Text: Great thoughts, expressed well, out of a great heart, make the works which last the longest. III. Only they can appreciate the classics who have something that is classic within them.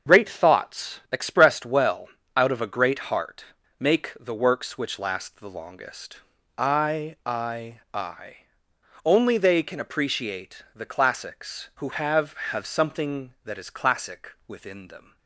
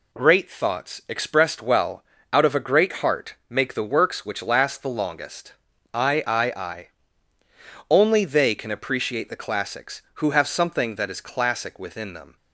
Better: second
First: starts louder than the rest; until 1.1 s; 6.5 dB // says "have" twice; at 12.5 s // pauses between "classic" and "within"; slight; at 14.3 s; 0.16 s long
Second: none

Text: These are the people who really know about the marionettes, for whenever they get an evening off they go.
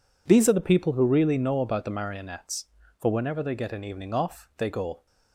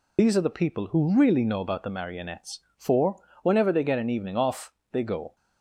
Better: first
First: none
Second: loses the start of "These"; at 0.1 s; 40 ms // pauses between "for" and "whenever"; slight; at 3.2 s; 0.20 s long // pauses between "off" and "they"; slight; at 4.7 s; 0.20 s long

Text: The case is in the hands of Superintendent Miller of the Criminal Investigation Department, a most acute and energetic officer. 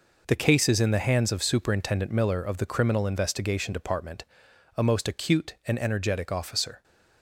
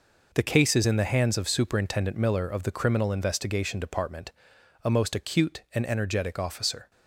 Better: neither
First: none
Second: none

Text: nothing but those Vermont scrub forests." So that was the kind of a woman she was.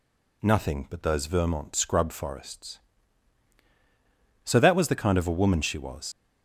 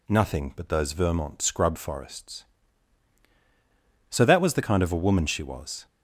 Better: second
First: leaves "was" unfinished; at 6.1 s; 85 ms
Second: none

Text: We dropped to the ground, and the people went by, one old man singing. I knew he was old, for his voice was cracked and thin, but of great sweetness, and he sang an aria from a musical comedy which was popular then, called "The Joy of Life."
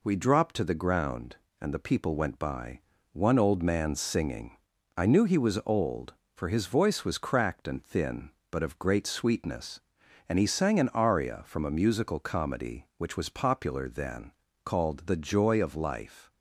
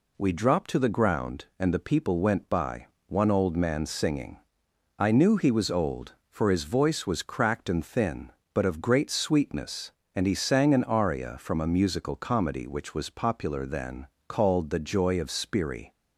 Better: first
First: none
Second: says "Spiri" for "Life"; at 15.3 s

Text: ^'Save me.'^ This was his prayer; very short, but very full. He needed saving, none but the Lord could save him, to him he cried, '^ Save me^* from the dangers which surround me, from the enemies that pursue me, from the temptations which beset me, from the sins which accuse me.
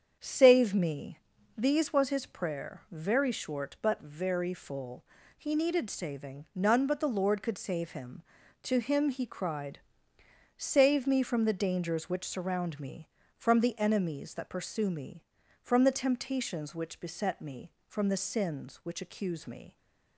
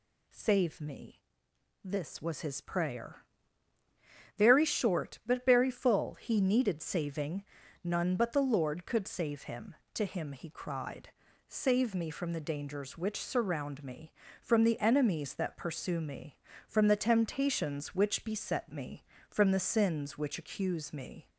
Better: second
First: starts louder than the rest; strong; until 1.6 s; 7.5 dB // says "These" for "This"; at 1.5 s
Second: none

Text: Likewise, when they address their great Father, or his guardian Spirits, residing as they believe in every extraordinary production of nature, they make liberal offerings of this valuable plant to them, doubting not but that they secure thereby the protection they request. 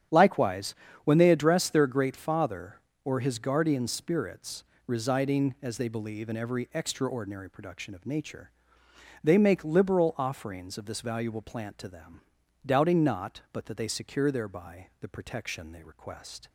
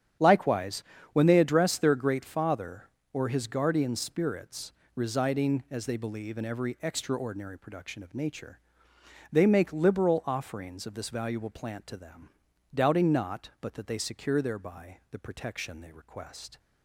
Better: neither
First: starts louder than the rest; strong; until 1.4 s; 9.5 dB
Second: starts louder than the rest; strong; until 1.4 s; 9.5 dB

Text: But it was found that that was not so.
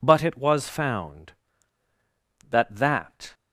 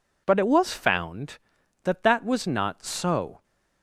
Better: second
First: stops before "was not so"; at 3.3 s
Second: none

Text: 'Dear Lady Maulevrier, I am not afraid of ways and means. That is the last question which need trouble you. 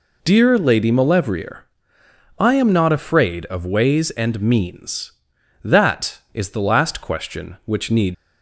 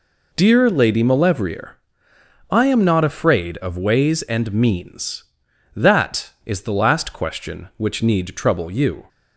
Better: second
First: stops before "trouble you"; at 8.1 s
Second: none

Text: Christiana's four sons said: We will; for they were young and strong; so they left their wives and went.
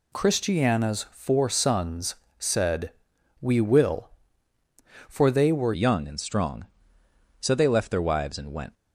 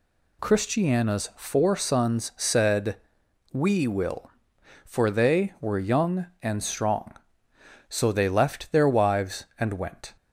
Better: second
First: pauses between "sons" and "said"; slight; at 2.1 s; 0.22 s long // changes voice at "young"; from 5.7 s on; 3.0 s long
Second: none

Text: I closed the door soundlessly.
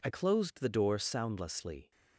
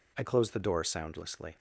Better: second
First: changes voice at "closed"; from 0.0 s on; 1.9 s long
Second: none

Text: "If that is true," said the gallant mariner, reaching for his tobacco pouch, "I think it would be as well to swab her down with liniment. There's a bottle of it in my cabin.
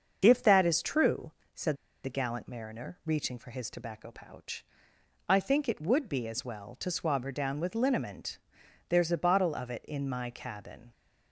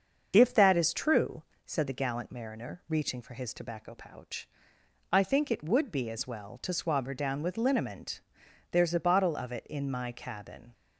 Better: second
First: starts louder than the rest; until 1.2 s; 6.5 dB // pauses between "said" and "the"; slight; at 1.7 s; 0.28 s long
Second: starts louder than the rest; until 1.3 s; 6.5 dB

